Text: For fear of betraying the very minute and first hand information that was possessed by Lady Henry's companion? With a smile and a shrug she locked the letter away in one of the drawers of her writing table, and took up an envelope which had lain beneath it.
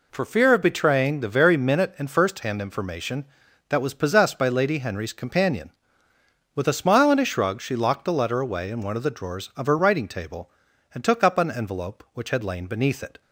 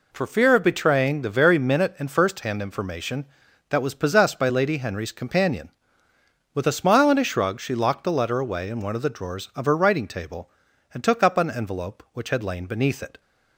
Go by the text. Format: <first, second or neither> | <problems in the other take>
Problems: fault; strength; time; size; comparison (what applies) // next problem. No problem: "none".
neither | none